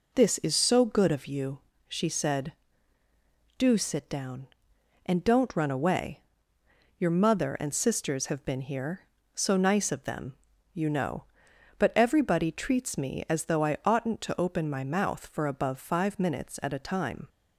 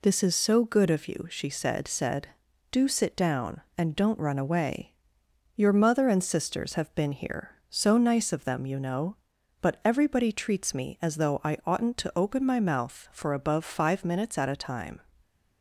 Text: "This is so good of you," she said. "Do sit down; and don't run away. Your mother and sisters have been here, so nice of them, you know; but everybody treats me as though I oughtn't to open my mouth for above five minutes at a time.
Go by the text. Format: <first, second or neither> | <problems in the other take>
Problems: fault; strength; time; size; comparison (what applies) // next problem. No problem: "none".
first | says "said" twice; at 1.8 s